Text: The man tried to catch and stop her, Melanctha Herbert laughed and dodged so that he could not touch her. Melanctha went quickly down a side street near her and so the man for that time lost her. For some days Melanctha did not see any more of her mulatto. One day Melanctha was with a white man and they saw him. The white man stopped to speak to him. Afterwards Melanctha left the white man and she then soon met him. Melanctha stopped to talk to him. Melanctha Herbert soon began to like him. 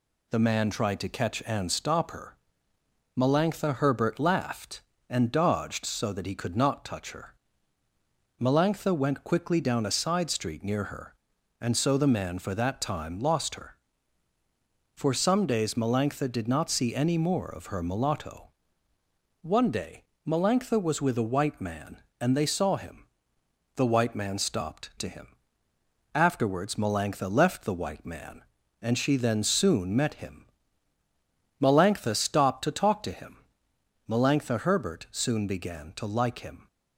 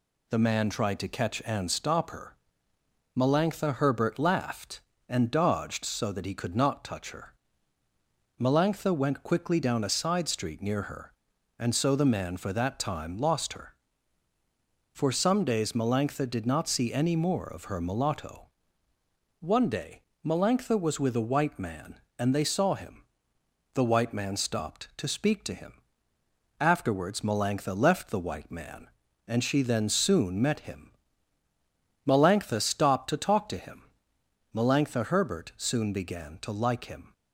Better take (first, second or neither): second